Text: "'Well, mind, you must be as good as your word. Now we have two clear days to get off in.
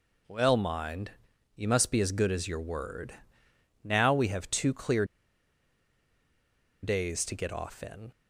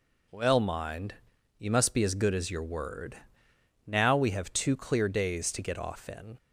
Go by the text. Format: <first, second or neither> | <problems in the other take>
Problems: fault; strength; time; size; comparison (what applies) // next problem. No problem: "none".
second | pauses between "clear" and "days"; strong; at 5.0 s; 1.7 s long